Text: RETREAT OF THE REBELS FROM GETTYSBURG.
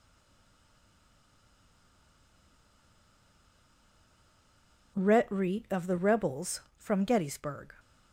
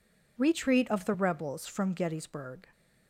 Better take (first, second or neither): second